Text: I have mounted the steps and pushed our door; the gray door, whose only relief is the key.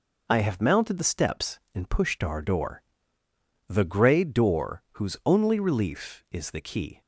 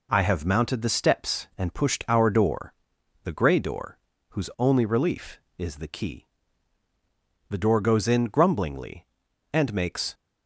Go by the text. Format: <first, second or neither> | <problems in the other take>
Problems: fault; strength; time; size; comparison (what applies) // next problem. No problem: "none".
first | goes on to say "The door goes in grumblingly and makes"; strong; from 7.4 s on; 2.6 s long